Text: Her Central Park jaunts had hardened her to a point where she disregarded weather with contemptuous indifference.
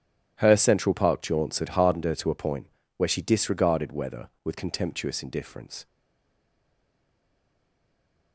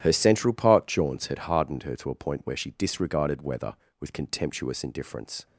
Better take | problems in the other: second | starts louder than the rest; strong; until 1.4 s; 11 dB; strong in the second // pauses between "point" and "where"; slight; at 2.6 s; 0.30 s long // stays silent after the last word; from 5.8 s on; 2.5 s long

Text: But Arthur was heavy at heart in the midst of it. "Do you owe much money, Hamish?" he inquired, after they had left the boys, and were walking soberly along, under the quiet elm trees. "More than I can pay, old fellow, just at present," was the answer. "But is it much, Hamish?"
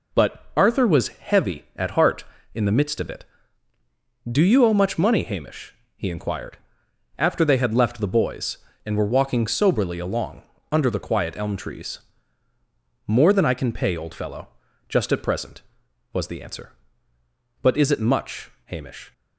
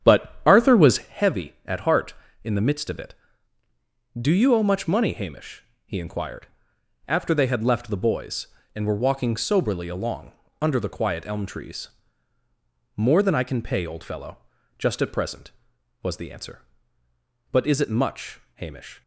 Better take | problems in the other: first | starts louder than the rest; strong; until 1.1 s; 9 dB

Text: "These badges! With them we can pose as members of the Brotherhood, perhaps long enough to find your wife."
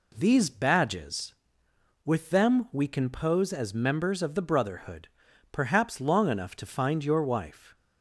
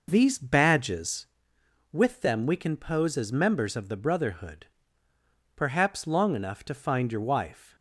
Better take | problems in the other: first | starts louder than the rest; noticeable; until 1.3 s; 5.5 dB

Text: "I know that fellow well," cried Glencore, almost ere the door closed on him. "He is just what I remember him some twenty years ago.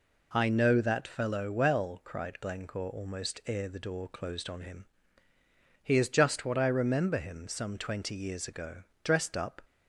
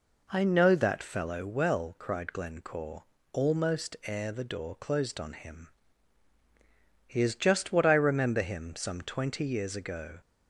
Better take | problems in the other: second | goes on to say "Dressed up"; from 9.0 s on; 0.56 s long

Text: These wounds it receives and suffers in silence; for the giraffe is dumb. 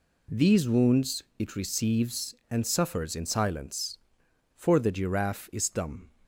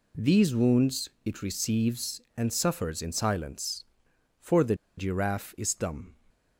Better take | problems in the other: first | pauses between "wounds" and "it"; slight; at 1.0 s; 0.16 s long; slight in the first // pauses between "the" and "giraffe"; slight; at 4.7 s; 0.23 s long

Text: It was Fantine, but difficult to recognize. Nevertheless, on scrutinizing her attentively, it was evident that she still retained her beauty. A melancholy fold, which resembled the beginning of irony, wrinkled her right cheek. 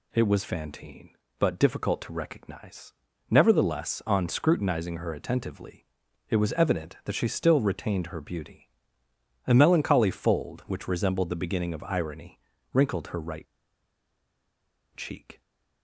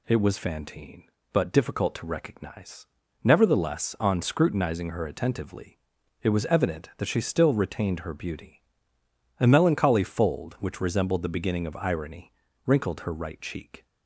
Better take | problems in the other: second | pauses between "right" and "cheek"; strong; at 13.4 s; 1.5 s long

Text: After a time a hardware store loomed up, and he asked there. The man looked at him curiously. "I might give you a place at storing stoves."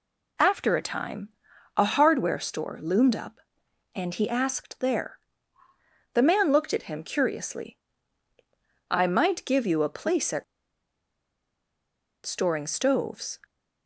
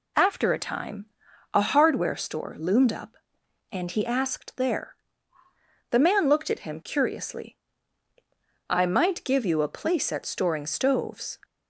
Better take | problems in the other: second | pauses between "time" and "a"; noticeable; at 1.2 s; 0.48 s long; noticeable in the second // pauses between "at" and "storing"; strong; at 10.4 s; 1.8 s long

